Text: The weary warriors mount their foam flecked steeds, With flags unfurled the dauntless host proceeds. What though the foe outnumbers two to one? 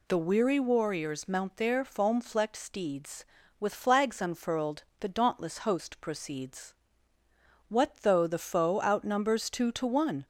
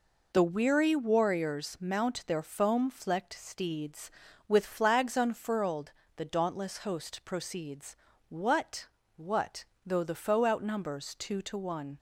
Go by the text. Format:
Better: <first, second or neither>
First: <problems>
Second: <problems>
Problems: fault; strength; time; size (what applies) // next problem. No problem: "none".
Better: first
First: pauses between "unfurled" and "the"; slight; at 4.8 s; 0.16 s long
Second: pauses between "unfurled" and "the"; slight; at 5.9 s; 0.24 s long // says "What" twice; at 9.1 s